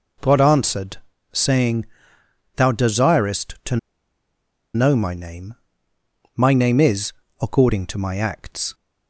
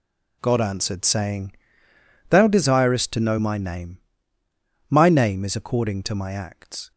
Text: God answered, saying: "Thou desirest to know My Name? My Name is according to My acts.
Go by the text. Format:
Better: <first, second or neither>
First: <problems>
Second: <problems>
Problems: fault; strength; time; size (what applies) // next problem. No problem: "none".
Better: second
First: pauses between "to" and "know"; noticeable; at 3.7 s; 0.97 s long // pauses between "is" and "according"; slight; at 7.1 s; 0.28 s long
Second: none